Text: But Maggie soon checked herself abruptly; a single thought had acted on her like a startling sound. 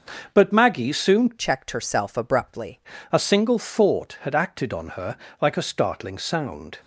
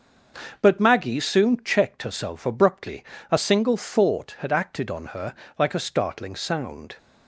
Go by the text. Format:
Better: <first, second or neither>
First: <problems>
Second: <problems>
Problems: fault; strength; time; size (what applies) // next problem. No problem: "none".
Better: second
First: starts louder than the rest; until 1.3 s; 6 dB // changes voice from "checked" to "abruptly"; from 1.3 to 2.7 s; 1.4 s long // pauses between "her" and "like"; slight; at 5.1 s; 0.24 s long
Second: starts louder than the rest; until 1.6 s; 6 dB // pauses between "her" and "like"; slight; at 5.3 s; 0.24 s long